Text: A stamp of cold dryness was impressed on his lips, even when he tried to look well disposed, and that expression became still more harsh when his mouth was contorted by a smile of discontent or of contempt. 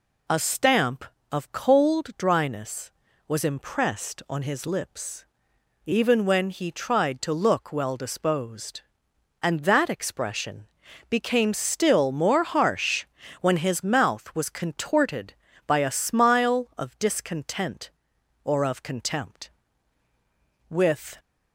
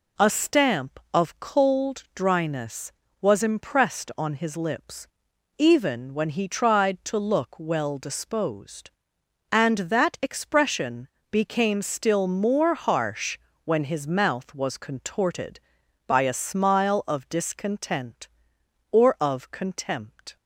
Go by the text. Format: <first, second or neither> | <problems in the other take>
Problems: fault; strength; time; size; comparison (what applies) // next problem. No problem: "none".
second | pauses between "expression" and "became"; at 10.6 s; 0.42 s long; slight in the second // pauses between "harsh" and "when"; slight; at 13.0 s; 0.36 s long; slight in the second // goes on to say "With"; slight; from 20.6 s on; 0.48 s long